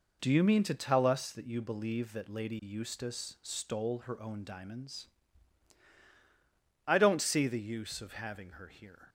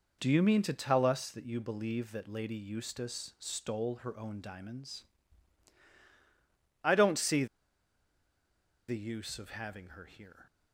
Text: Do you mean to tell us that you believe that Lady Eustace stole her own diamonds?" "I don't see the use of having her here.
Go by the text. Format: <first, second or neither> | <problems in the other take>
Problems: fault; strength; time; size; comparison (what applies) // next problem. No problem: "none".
first | pauses between "see" and "the"; strong; at 7.4 s; 1.4 s long